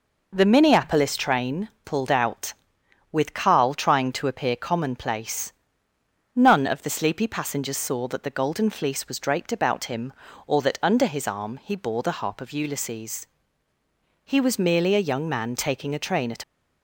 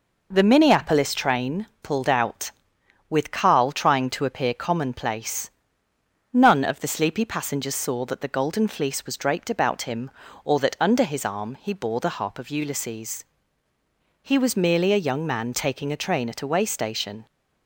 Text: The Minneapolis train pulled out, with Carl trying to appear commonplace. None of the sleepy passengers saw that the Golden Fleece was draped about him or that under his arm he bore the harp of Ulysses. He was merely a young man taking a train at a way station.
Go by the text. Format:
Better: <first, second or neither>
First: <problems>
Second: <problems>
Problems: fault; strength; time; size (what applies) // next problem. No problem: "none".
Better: second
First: pauses between "train" and "pulled"; slight; at 1.6 s; 0.16 s long // stops before "a way station"; at 16.4 s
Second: pauses between "train" and "pulled"; slight; at 1.6 s; 0.16 s long